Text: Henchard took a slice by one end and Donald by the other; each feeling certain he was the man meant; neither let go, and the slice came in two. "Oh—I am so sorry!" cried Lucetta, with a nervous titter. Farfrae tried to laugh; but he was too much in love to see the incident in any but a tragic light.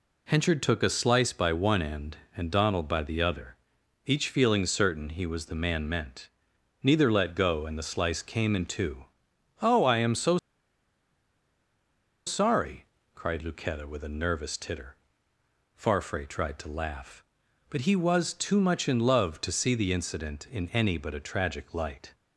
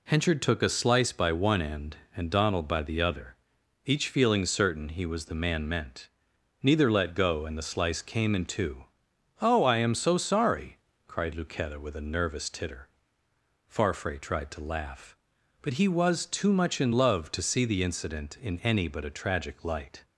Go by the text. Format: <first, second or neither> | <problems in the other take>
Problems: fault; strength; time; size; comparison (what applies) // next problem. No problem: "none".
second | pauses between "so" and "sorry"; strong; at 10.3 s; 1.8 s long